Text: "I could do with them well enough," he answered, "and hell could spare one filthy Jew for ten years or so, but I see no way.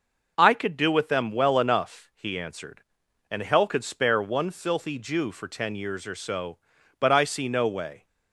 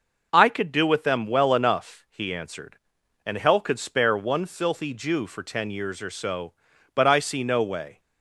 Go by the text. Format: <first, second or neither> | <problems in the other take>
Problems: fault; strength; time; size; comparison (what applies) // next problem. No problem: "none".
neither | none